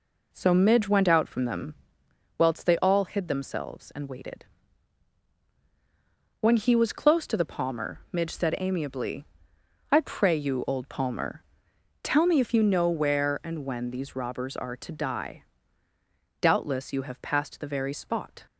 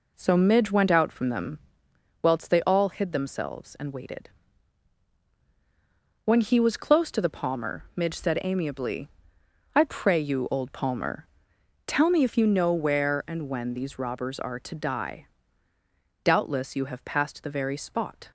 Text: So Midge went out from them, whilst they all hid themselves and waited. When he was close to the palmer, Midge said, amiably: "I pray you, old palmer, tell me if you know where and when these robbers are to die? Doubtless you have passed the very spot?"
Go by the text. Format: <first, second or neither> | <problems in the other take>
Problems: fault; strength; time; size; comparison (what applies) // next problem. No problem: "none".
neither | none